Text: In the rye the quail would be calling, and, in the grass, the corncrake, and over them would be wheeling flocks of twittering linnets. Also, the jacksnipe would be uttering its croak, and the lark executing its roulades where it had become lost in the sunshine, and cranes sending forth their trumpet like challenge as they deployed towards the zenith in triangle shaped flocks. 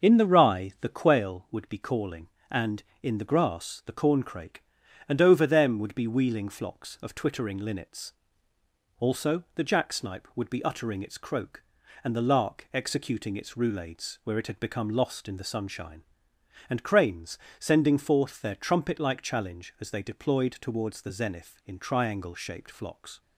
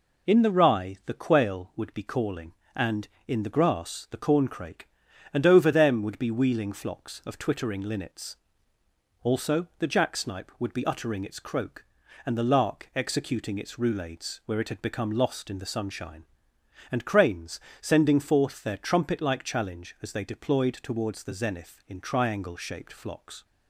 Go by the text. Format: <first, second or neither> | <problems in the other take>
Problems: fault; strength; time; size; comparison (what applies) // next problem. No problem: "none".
second | starts louder than the rest; until 1.2 s; 7 dB // pauses between "cranes" and "sending"; slight; at 17.3 s; 0.20 s long; slight in the second